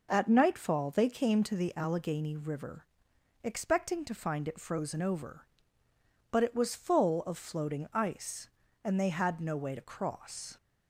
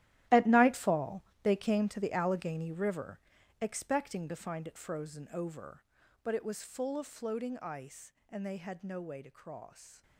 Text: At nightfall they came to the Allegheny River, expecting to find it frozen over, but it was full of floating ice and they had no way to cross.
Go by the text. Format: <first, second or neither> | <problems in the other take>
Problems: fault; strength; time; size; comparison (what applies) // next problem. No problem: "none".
first | gets quieter; strong; throughout; 14.5 dB // pauses between "nightfall" and "they"; slight; at 1.2 s; 0.22 s long